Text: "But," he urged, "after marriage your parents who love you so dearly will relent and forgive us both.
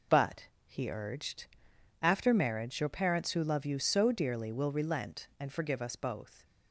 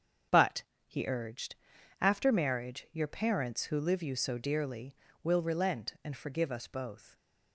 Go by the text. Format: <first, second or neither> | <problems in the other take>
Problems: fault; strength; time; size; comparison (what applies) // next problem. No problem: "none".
first | starts louder than the rest; strong; until 2.0 s; 7.5 dB // says "live" for "love"; at 3.7 s